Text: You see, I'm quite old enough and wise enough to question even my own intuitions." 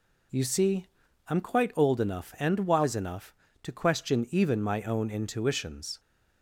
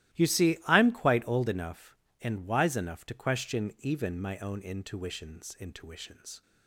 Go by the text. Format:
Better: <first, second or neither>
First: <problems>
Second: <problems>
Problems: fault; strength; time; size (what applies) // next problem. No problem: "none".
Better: first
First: none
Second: starts louder than the rest; strong; until 1.2 s; 15.5 dB // says "intuitions" twice; at 5.5 s